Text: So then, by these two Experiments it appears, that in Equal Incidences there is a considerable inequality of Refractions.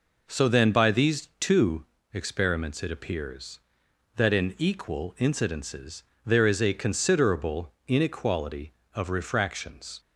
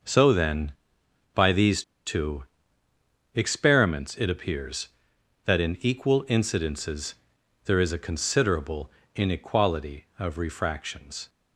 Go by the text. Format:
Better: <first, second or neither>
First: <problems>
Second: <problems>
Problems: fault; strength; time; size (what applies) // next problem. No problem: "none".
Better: first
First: pauses between "two" and "Experiments"; slight; at 1.8 s; 0.26 s long // pauses between "Incidences" and "there"; slight; at 6.0 s; 0.22 s long // pauses between "considerable" and "inequality"; slight; at 7.7 s; 0.16 s long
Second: pauses between "these" and "two"; slight; at 1.8 s; 0.24 s long // pauses between "two" and "Experiments"; noticeable; at 2.4 s; 0.90 s long // pauses between "Incidences" and "there"; noticeable; at 7.1 s; 0.50 s long // pauses between "considerable" and "inequality"; slight; at 8.9 s; 0.24 s long